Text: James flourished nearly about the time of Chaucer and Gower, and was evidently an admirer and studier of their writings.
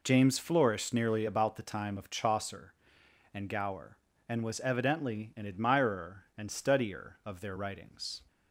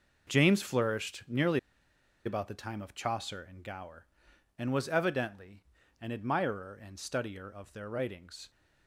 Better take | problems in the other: first | pauses between "nearly" and "about"; noticeable; at 1.5 s; 0.67 s long // pauses between "evidently" and "an"; slight; at 5.6 s; 0.36 s long

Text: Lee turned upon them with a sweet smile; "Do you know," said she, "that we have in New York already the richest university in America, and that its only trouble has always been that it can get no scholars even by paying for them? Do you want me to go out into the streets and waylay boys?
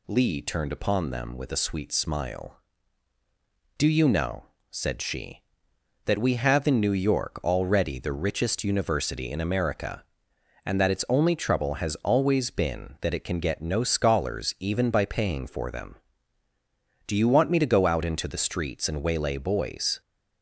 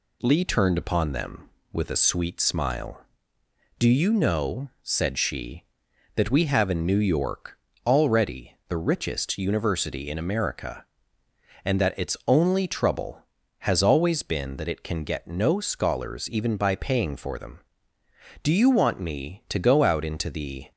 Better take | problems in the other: first | pauses between "York" and "already"; slight; at 7.5 s; 0.30 s long // stops before "streets and waylay boys"; at 20.7 s

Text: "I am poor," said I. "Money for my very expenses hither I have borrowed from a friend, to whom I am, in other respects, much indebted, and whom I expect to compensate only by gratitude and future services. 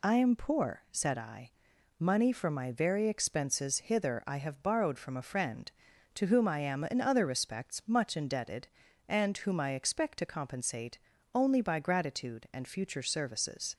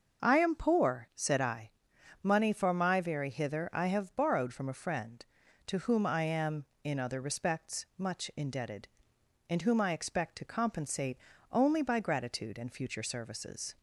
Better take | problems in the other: first | starts louder than the rest; until 1.3 s; 6 dB // skips "expenses"; at 3.2 s // pauses between "compensate" and "only"; slight; at 11.1 s; 0.34 s long; slight in the first

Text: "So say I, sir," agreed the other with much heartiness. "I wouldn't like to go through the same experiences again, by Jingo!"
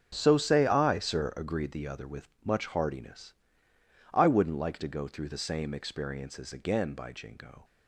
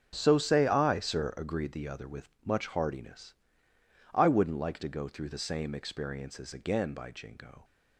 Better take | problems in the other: neither | starts louder than the rest; the same in both // pauses between "with" and "much"; slight; the same in both

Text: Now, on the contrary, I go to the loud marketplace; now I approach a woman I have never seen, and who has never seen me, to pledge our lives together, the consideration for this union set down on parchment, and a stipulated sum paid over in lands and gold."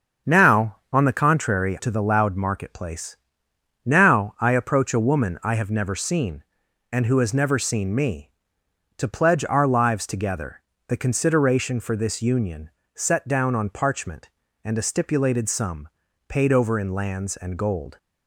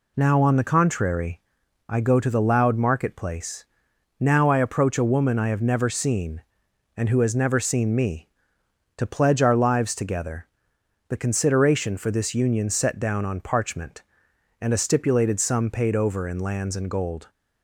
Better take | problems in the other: second | starts louder than the rest; until 1.4 s; 7 dB // skips "I go"; at 1.7 s // pauses between "union" and "set"; slight; at 12.6 s; 0.24 s long // pauses between "sum" and "paid"; at 15.8 s; 0.40 s long

